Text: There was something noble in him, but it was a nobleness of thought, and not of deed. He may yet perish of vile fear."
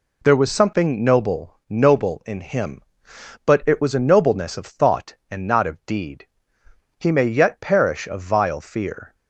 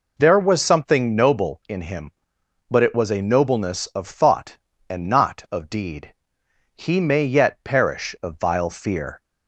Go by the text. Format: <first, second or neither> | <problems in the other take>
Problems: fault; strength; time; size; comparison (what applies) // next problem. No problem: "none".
second | says "noble" twice; at 1.6 s